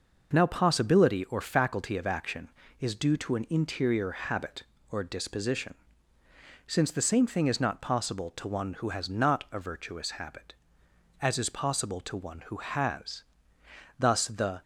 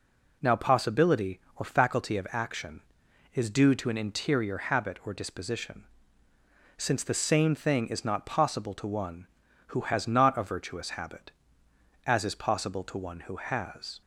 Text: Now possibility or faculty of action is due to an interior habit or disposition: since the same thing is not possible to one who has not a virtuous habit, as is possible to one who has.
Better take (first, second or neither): second